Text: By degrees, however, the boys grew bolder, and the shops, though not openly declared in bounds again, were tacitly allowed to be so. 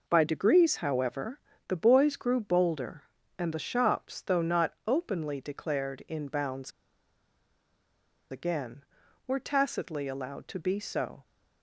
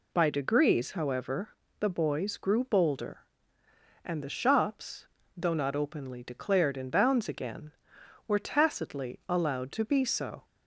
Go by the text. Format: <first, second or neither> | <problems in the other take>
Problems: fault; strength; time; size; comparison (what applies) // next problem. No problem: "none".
second | pauses between "bounds" and "again"; strong; at 6.7 s; 1.6 s long